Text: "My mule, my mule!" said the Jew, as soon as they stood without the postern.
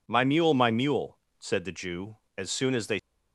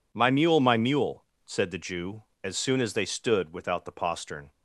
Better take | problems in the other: second | stops before "stood without the postern"; at 2.9 s

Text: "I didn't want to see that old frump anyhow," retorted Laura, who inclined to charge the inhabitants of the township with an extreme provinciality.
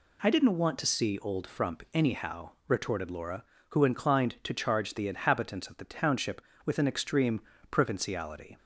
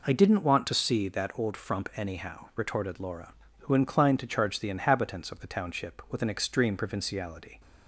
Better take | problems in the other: second | skips "that"; at 1.1 s // pauses between "extreme" and "provinciality"; slight; at 7.4 s; 0.30 s long

